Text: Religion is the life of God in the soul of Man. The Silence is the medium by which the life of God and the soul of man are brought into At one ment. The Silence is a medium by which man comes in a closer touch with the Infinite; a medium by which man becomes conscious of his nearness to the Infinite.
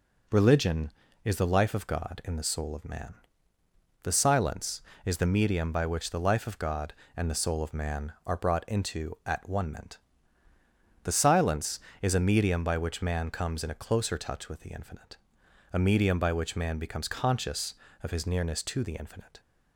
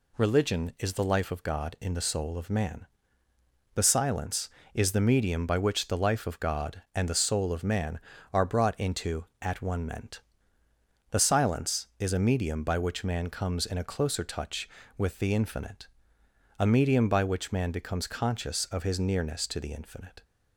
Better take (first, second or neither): neither